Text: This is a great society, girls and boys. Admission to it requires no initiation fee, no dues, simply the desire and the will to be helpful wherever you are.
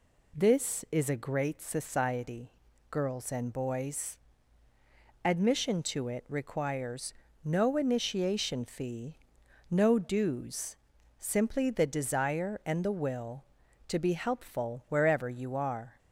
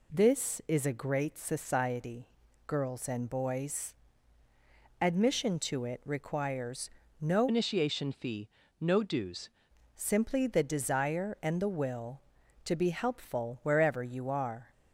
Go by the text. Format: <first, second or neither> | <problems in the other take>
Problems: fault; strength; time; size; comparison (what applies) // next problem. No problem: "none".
first | pauses between "requires" and "no"; slight; at 6.8 s; 0.32 s long; slight in the first // changes voice from "initiation" to "dues"; from 7.4 to 9.4 s; 2.0 s long